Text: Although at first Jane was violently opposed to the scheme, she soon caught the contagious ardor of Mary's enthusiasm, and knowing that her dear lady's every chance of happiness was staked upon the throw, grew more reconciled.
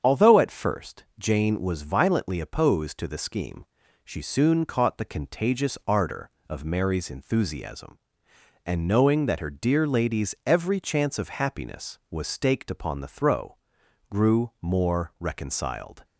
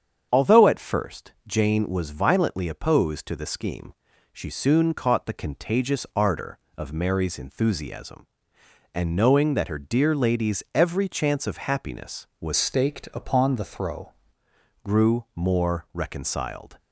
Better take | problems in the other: first | starts louder than the rest; strong; until 1.3 s; 7.5 dB; strong in the first // changes voice from "staked" to "throw"; from 12.5 to 14.1 s; 1.6 s long

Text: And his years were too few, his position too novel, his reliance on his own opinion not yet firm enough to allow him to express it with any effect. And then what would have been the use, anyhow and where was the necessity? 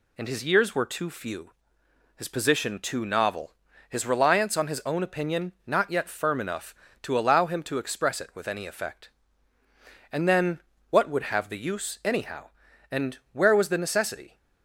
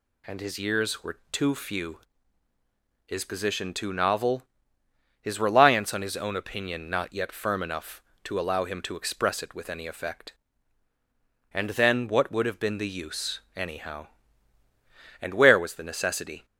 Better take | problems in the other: second | pauses between "then" and "what"; slight; at 10.6 s; 0.30 s long // skips "been"; at 11.4 s // pauses between "and" and "where"; slight; at 13.1 s; 0.16 s long

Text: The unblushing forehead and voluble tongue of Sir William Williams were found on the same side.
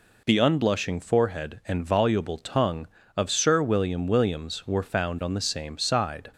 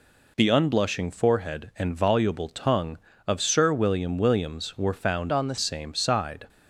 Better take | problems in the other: first | changes voice from "on" to "the"; from 5.3 to 5.5 s; 0.2 s long

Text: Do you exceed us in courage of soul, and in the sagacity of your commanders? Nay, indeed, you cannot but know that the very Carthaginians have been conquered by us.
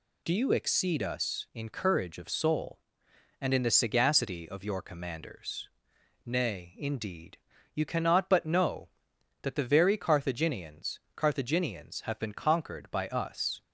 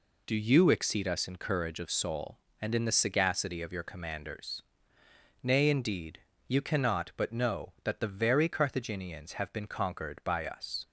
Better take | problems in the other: second | says "Carthaginians" twice; at 11.1 s

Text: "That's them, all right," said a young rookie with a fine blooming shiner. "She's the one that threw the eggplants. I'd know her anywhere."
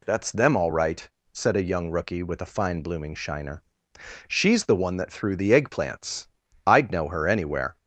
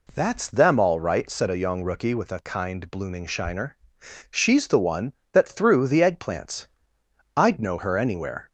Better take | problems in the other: first | says "kind" for "fine"; at 2.4 s

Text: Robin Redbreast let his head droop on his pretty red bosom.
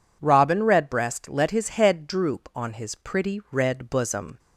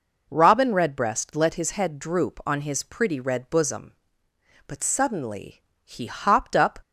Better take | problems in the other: first | goes on to say "But suddenly he hopped up"; strong; from 4.6 s on; 2.1 s long

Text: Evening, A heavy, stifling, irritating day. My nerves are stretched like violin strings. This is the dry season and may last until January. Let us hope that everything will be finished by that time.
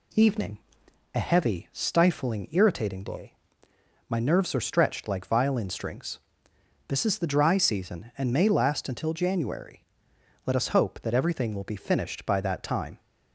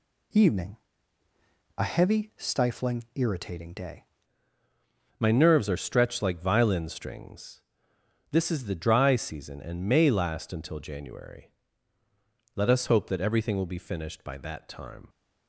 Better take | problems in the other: first | changes voice at "My"; from 5.1 s on; 9.9 s long

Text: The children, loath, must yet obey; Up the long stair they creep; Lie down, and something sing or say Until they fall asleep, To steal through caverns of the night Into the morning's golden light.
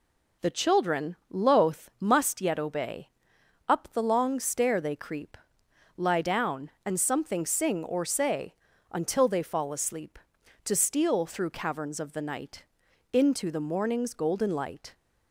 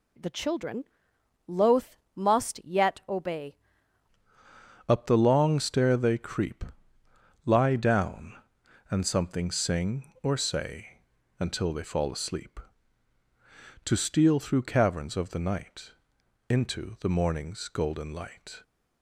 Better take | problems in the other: first | changes voice at "Up"; from 4.8 s on; 13.8 s long // pauses between "say" and "Until"; slight; at 11.0 s; 0.36 s long; also in the first // pauses between "night" and "Into"; noticeable; at 15.9 s; 0.58 s long; noticeable in the first

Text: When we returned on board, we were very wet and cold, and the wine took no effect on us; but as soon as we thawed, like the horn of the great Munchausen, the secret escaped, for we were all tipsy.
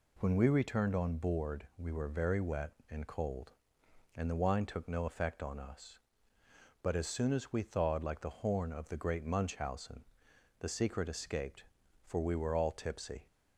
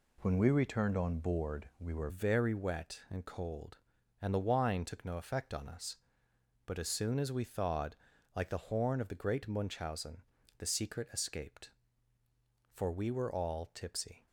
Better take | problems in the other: first | changes voice at "very"; from 2.0 s on; 12.2 s long

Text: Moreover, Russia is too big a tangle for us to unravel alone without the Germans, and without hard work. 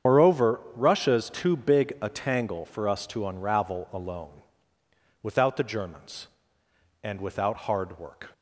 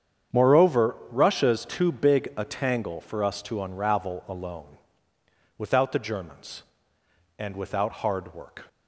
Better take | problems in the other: second | loses the start of "Moreover"; at 0.0 s; 80 ms // starts louder than the rest; strong; until 1.1 s; 8 dB; strong in the second // pauses between "alone" and "without"; noticeable; at 4.4 s; 0.80 s long; noticeable in the second

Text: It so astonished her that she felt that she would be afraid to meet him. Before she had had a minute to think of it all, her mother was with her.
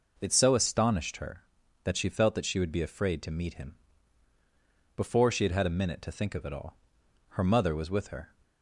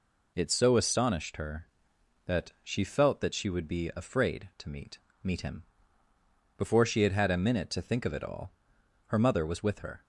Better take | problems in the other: first | says "meet" twice; at 5.2 s

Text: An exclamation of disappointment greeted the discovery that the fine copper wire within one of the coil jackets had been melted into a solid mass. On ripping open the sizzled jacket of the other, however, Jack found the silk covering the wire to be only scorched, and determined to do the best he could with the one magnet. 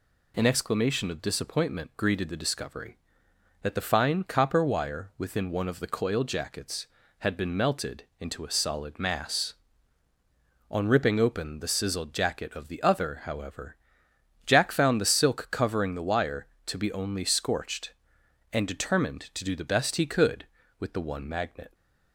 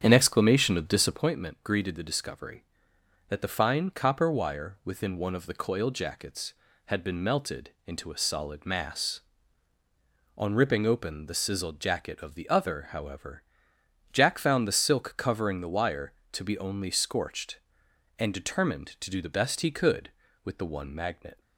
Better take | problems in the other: first | starts louder than the rest; strong; until 1.3 s; 8.5 dB // pauses between "melted" and "into"; slight; at 7.6 s; 0.16 s long; slight in the first

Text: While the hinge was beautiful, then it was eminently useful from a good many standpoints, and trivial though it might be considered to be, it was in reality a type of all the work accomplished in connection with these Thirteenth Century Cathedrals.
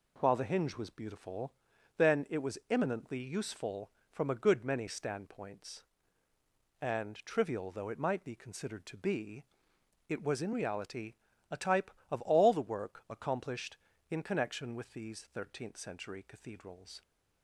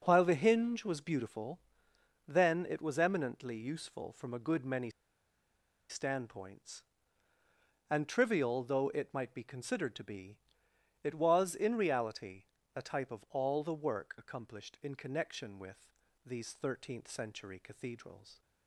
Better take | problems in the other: first | pauses between "many" and "standpoints"; at 4.8 s; 1.0 s long // pauses between "reality" and "a"; slight; at 12.4 s; 0.32 s long; slight in the first // pauses between "with" and "these"; slight; at 15.8 s; 0.36 s long

